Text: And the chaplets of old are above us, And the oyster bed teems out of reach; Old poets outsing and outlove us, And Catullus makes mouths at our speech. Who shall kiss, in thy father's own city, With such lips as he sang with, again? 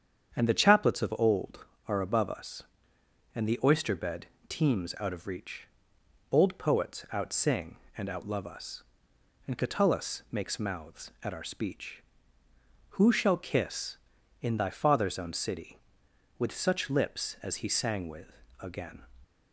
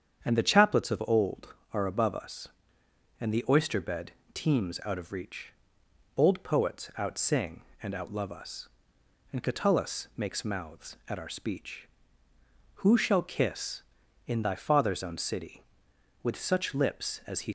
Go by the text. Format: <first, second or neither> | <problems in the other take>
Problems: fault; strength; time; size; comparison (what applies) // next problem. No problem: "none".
first | starts louder than the rest; strong; until 1.2 s; 8 dB; strong in the first // pauses between "bed" and "teems"; slight; at 4.1 s; 0.22 s long; slight in the first // stops before "sang with again"; at 17.4 s